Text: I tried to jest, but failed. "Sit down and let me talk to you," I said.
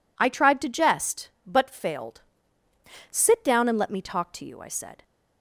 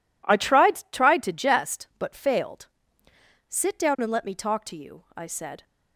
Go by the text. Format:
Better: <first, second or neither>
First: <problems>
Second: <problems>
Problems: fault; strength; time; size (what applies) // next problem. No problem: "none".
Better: first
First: none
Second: says "tried" twice; at 0.9 s